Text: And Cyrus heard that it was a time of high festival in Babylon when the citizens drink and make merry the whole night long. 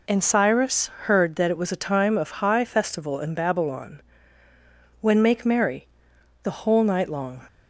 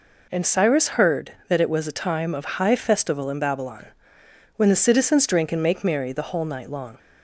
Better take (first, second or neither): second